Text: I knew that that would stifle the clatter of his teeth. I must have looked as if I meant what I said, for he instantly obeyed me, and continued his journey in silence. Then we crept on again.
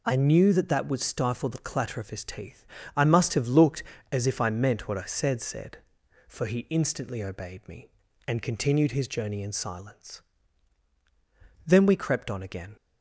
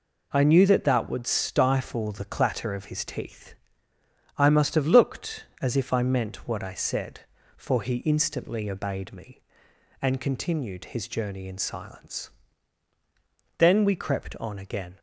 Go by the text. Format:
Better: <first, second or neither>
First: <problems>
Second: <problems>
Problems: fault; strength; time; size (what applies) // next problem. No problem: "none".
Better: second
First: says "said" twice; at 5.4 s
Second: none